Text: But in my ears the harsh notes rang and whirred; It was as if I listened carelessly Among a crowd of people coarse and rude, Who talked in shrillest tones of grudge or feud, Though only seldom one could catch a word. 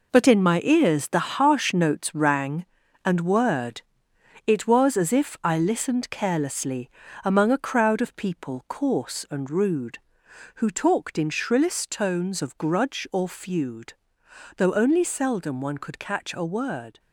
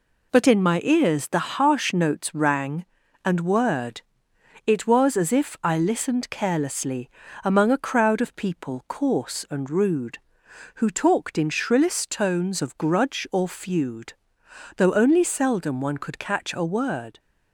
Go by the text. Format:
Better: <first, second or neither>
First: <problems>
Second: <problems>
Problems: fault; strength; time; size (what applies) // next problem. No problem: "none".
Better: second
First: gets quieter; strong; throughout; 8.5 dB // pauses between "carelessly" and "Among"; slight; at 6.8 s; 0.34 s long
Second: pauses between "carelessly" and "Among"; slight; at 7.0 s; 0.34 s long